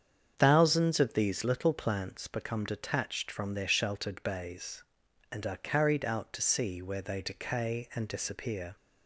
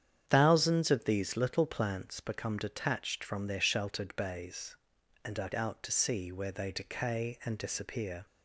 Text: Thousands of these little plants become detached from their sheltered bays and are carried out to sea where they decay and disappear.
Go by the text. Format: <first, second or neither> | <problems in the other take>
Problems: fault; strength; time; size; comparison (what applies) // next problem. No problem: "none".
first | starts louder than the rest; strong; until 1.2 s; 8.5 dB; strong in the first // skips "carried"; at 5.5 s